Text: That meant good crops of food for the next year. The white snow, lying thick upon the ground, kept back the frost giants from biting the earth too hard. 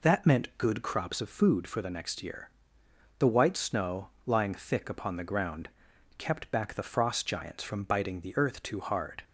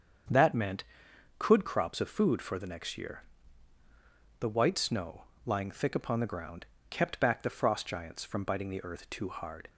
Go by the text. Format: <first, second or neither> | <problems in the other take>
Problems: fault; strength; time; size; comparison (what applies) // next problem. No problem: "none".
first | starts louder than the rest; strong; until 1.8 s; 7.5 dB // says "could" for "good"; at 1.3 s